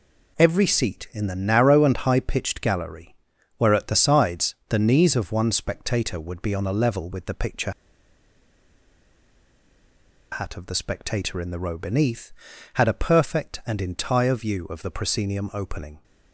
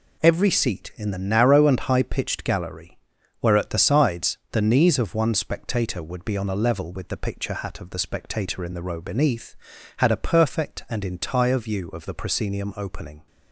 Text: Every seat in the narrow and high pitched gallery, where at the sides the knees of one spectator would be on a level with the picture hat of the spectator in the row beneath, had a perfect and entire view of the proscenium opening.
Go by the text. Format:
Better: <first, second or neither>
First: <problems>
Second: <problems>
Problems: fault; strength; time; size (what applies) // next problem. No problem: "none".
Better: second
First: pauses between "picture" and "hat"; strong; at 7.7 s; 2.6 s long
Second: none